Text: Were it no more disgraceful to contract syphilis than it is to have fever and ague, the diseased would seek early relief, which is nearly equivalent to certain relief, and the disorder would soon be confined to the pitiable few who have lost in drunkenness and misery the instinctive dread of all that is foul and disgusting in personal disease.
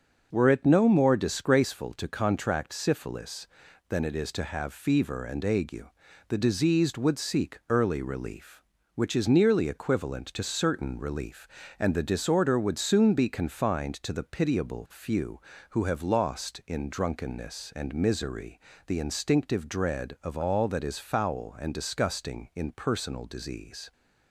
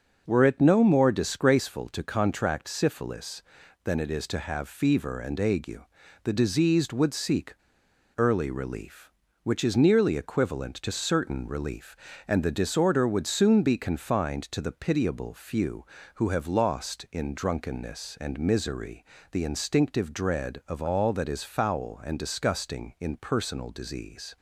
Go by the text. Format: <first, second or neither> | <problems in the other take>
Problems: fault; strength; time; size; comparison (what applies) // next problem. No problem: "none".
first | starts louder than the rest; noticeable; until 1.2 s; 6 dB; noticeable in the first // pauses between "seek" and "early"; noticeable; at 7.5 s; 0.63 s long // pauses between "misery" and "the"; slight; at 19.0 s; 0.30 s long; slight in the first